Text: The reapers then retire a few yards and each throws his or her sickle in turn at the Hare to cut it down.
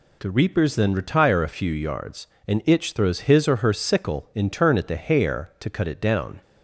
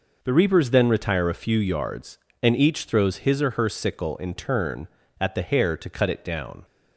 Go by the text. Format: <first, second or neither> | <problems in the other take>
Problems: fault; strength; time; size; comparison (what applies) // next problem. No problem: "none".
second | says "itch" for "each"; at 2.6 s